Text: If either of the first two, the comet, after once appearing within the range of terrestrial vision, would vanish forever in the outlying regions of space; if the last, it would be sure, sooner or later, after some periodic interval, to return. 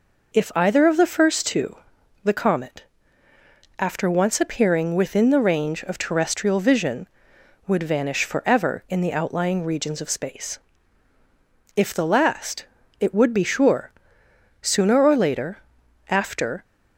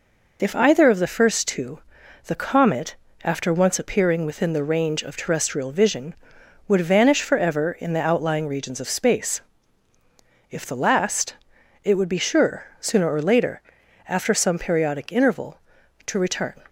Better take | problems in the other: second | stops before "some periodic interval to return"; at 16.6 s

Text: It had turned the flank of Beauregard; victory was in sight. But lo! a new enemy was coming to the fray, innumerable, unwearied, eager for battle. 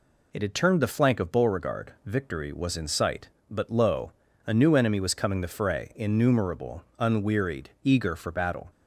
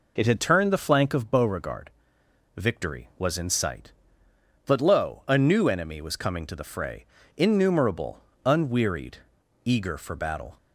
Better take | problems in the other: second | skips "to"; at 5.4 s

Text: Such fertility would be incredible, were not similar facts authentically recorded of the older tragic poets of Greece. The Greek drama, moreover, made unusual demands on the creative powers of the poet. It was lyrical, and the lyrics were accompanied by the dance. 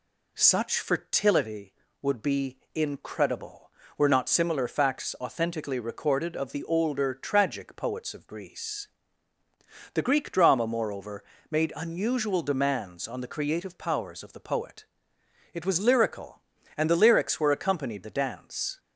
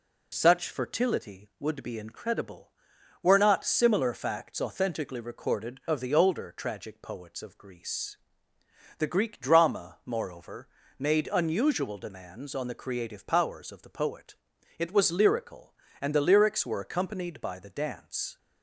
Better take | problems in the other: second | pauses between "be" and "incredible"; slight; at 2.5 s; 0.16 s long // skips "by"; at 18.0 s

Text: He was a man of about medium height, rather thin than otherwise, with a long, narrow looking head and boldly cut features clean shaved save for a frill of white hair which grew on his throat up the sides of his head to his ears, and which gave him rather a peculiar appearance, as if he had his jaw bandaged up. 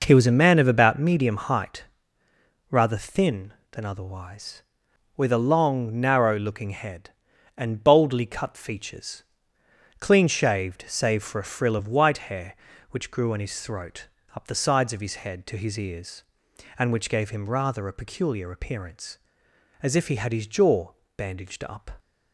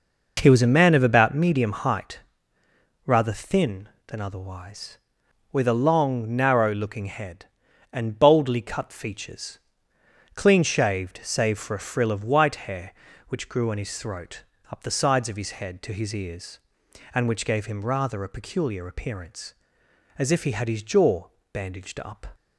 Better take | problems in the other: neither | pauses between "features" and "clean"; noticeable; the same in both // pauses between "throat" and "up"; slight; the same in both // pauses between "jaw" and "bandaged"; slight; the same in both

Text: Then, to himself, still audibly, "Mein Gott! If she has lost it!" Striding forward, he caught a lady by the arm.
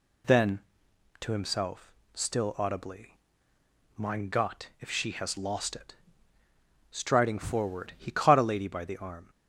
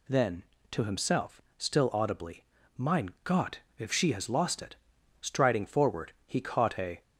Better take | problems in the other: first | stops before "lady by the arm"; at 7.0 s

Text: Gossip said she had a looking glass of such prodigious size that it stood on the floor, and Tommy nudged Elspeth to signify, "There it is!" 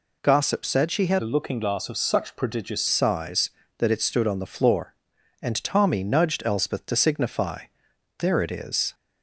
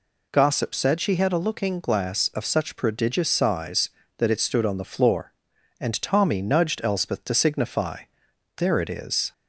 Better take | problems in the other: second | changes voice from "a" to "prodigious"; from 1.2 to 2.8 s; 1.6 s long

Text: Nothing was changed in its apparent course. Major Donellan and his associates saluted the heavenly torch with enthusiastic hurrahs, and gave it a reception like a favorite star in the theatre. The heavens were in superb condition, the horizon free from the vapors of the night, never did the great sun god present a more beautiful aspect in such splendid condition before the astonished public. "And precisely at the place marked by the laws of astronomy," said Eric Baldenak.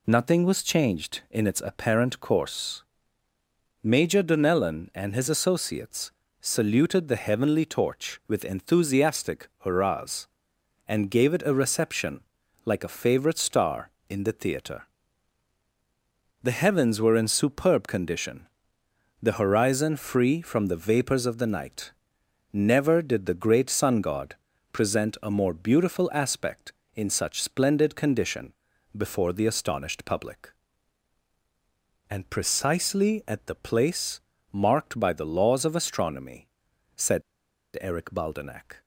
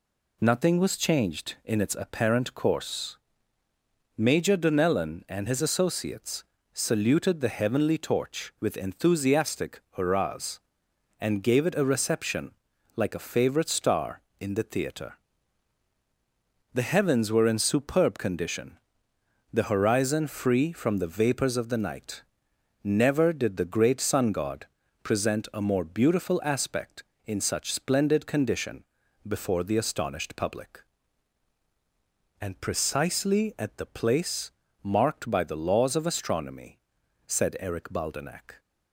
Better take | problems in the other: second | pauses between "associates" and "saluted"; slight; at 6.1 s; 0.32 s long; slight in the second // pauses between "reception" and "like"; noticeable; at 12.2 s; 0.46 s long; noticeable in the second // pauses between "god" and "present"; slight; at 24.3 s; 0.36 s long; slight in the second // pauses between "condition" and "before"; at 28.5 s; 0.42 s long; also in the second // pauses between "place" and "marked"; slight; at 34.2 s; 0.32 s long; slight in the second // pauses between "said" and "Eric"; noticeable; at 37.2 s; 0.58 s long

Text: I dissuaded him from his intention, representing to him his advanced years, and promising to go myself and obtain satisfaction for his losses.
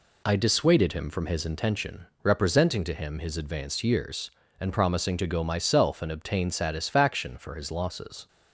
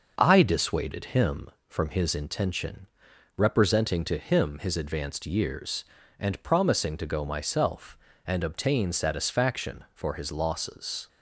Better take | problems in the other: neither | none

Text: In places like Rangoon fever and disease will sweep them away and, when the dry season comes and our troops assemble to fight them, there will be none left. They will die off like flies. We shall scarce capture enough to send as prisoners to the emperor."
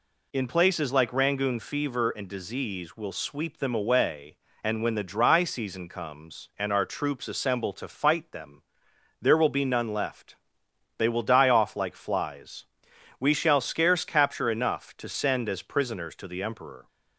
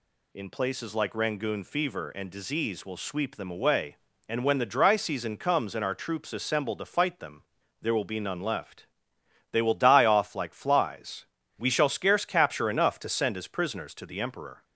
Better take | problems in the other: neither | none

